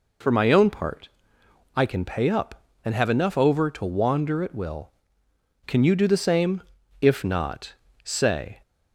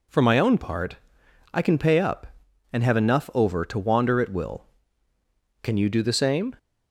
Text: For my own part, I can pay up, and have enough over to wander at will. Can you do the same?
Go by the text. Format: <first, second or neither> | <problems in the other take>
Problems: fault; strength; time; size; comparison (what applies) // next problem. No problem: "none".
second | goes on to say "If not say"; from 7.0 s on; 1.6 s long